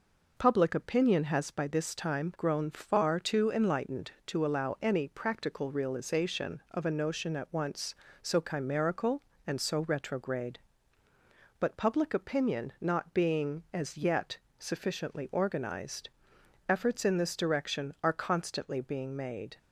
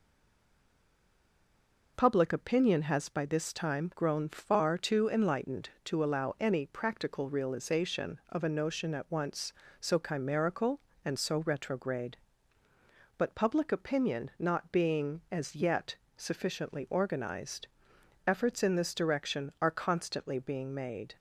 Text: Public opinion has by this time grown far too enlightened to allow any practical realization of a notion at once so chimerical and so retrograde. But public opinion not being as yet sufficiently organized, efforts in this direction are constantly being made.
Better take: first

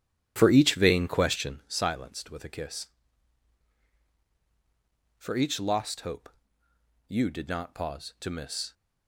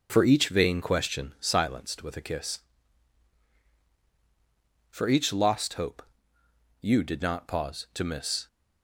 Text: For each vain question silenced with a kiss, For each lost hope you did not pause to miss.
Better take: second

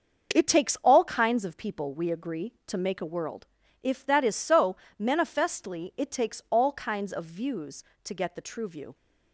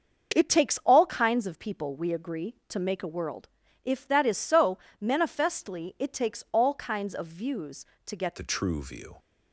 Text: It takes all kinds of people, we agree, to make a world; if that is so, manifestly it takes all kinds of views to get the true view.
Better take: first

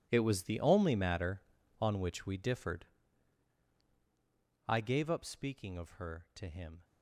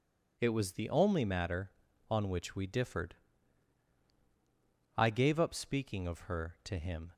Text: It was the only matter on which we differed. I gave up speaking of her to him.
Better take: second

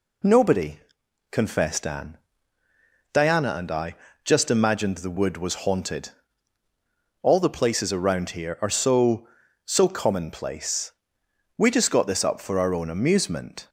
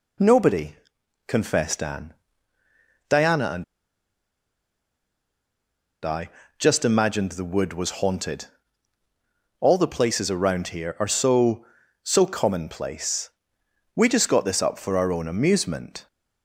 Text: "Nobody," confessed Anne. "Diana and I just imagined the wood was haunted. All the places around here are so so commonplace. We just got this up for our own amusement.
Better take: first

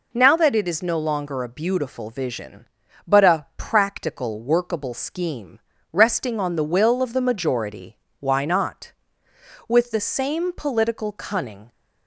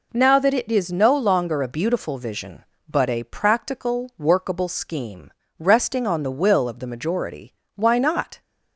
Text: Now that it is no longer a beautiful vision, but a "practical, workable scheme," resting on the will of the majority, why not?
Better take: second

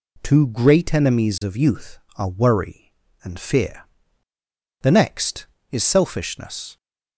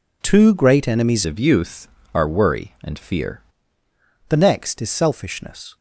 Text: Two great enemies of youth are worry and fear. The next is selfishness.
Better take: first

